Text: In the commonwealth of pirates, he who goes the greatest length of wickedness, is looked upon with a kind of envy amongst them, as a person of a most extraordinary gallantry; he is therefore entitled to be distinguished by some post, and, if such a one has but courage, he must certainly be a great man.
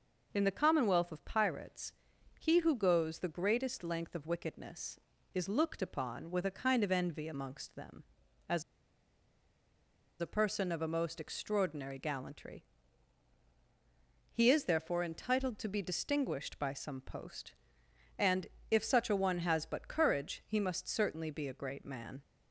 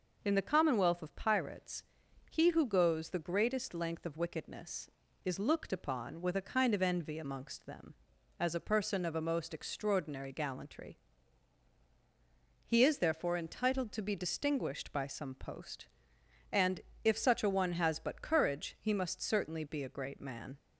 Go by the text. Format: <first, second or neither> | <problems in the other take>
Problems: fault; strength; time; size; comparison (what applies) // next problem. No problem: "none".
second | pauses between "as" and "a"; strong; at 8.6 s; 1.5 s long